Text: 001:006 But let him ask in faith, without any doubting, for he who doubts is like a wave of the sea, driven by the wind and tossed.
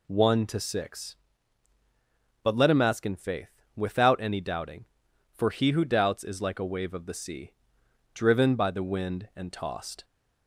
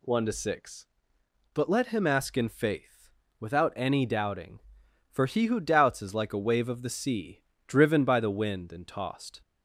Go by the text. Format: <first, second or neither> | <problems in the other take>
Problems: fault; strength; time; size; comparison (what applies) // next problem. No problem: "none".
neither | none